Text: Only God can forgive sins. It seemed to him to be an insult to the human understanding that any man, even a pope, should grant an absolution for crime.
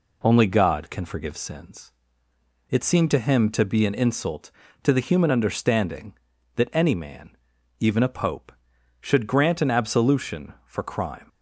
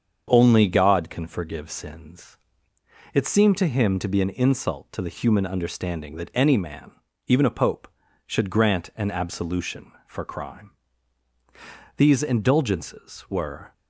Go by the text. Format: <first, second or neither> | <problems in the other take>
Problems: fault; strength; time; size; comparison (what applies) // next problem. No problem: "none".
first | starts louder than the rest; until 1.3 s; 7 dB // goes on to say "These indulgences were"; strong; from 11.9 s on; 1.7 s long